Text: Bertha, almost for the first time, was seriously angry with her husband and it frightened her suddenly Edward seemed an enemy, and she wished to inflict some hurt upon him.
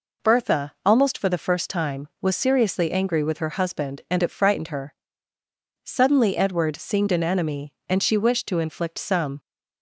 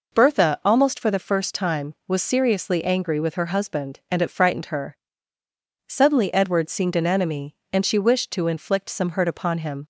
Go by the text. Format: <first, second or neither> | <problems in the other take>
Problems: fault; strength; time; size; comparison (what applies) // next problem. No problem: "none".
second | pauses between "her" and "suddenly"; noticeable; at 4.9 s; 0.88 s long; noticeable in the second // stops before "hurt upon him"; at 9.3 s